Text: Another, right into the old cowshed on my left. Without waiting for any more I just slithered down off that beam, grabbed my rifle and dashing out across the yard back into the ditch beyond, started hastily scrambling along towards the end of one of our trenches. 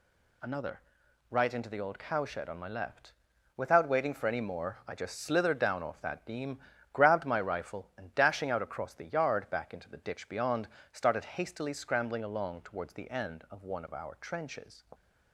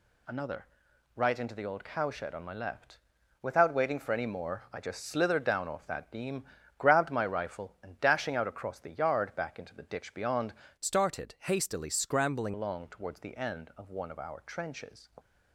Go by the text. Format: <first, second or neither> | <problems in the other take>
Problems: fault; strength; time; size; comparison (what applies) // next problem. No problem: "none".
first | changes voice from "started" to "scrambling"; from 10.7 to 12.5 s; 1.8 s long